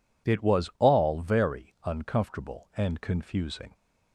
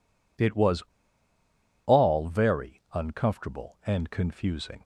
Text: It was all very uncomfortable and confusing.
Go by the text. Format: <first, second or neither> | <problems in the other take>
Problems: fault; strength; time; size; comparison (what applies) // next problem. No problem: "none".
first | pauses between "was" and "all"; at 0.8 s; 1.0 s long